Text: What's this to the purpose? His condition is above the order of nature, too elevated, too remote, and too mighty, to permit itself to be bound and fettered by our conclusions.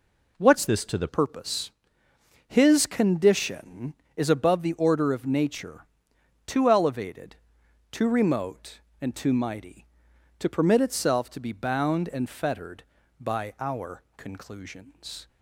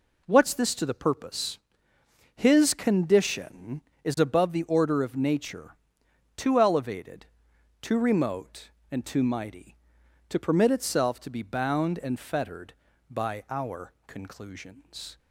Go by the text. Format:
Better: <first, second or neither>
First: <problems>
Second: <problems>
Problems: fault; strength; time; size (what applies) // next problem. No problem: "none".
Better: second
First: changes voice from "this" to "the"; from 0.6 to 1.0 s; 0.4 s long // pauses between "our" and "conclusions"; slight; at 14.0 s; 0.16 s long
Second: pauses between "our" and "conclusions"; slight; at 13.9 s; 0.16 s long